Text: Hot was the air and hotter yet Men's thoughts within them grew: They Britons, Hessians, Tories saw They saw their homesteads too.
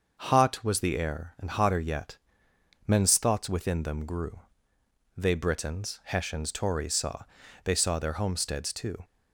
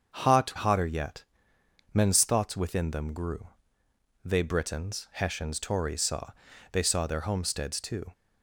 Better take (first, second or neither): first